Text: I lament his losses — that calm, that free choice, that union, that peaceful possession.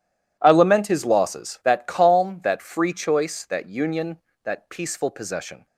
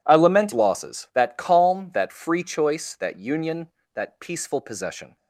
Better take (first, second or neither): first